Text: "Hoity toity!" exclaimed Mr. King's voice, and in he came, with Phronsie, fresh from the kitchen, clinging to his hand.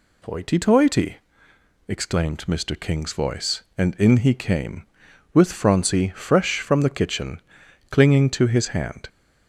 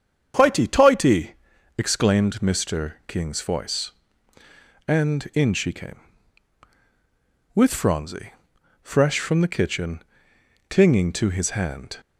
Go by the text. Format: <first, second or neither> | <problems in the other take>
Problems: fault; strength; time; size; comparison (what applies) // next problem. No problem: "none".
first | starts louder than the rest; strong; until 1.8 s; 7.5 dB // says "she" for "he"; at 5.5 s